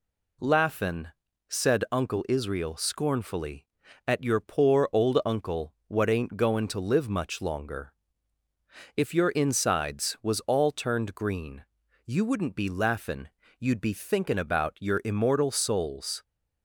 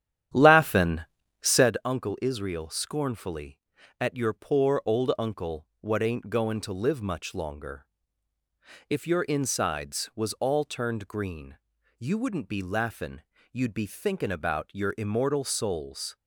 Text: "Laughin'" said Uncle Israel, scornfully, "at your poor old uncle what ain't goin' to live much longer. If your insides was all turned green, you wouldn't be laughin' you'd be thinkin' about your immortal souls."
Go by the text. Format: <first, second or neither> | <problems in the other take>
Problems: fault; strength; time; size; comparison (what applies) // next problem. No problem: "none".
first | starts louder than the rest; strong; until 1.7 s; 10.5 dB // pauses between "Laughin" and "said"; at 1.0 s; 0.40 s long; also in the first // pauses between "laughin" and "you'd"; slight; at 13.2 s; 0.28 s long; slight in the first